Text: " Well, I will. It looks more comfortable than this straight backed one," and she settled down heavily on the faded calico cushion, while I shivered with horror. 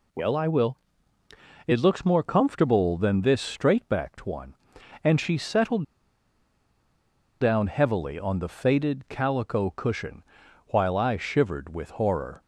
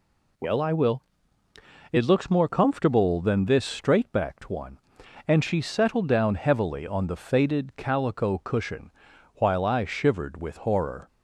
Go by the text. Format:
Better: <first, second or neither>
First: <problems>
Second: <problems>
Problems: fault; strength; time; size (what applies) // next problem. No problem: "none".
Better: second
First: pauses between "settled" and "down"; strong; at 5.8 s; 1.5 s long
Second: none